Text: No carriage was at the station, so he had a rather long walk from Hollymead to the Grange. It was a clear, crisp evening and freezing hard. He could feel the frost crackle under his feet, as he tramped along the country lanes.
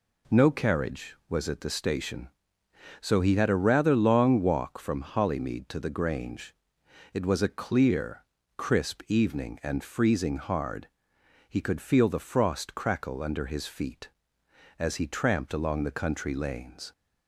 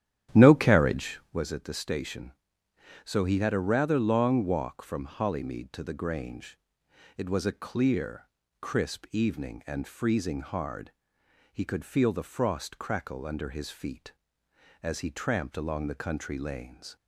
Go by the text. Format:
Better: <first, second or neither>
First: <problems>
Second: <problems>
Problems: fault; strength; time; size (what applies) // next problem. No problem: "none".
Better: first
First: none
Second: starts louder than the rest; strong; until 1.4 s; 11 dB